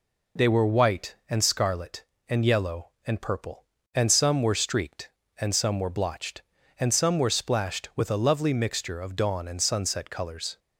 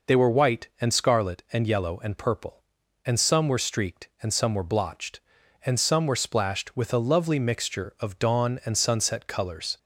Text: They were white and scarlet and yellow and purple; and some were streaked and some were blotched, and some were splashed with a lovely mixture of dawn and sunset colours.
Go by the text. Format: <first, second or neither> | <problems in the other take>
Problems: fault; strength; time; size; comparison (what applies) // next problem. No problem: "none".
neither | none